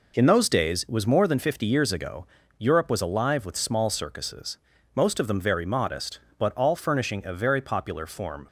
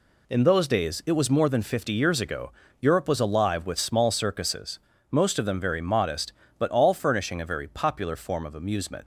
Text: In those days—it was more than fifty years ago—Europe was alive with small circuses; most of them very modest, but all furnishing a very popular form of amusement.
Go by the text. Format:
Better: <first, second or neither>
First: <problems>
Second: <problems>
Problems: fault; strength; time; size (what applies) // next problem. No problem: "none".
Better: second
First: stops before "of amusement"; at 8.4 s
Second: none